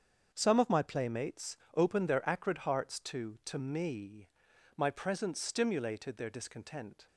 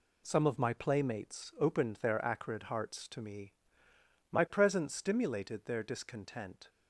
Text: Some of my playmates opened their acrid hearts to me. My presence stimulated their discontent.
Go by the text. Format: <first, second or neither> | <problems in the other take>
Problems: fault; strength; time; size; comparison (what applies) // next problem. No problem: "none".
second | starts louder than the rest; strong; until 1.3 s; 7 dB // pauses between "playmates" and "opened"; slight; at 1.5 s; 0.18 s long // says "to" twice; at 3.4 s